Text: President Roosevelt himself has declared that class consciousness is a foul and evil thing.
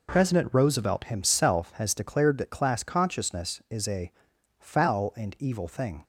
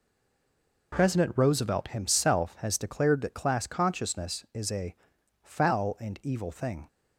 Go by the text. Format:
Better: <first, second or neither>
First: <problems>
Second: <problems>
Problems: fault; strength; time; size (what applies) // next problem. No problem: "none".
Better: first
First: pauses between "a" and "foul"; noticeable; at 4.0 s; 0.48 s long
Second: stays silent before the first word; slight; until 0.9 s; 0.9 s long // pauses between "a" and "foul"; noticeable; at 4.9 s; 0.48 s long